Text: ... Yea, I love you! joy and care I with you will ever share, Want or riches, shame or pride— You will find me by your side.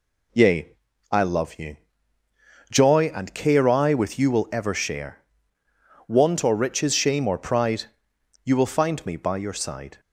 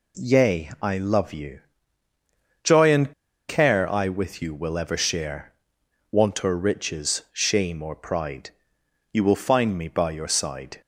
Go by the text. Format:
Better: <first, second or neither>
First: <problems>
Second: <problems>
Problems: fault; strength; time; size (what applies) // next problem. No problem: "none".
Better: first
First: none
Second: pauses between "and" and "care"; at 3.1 s; 0.36 s long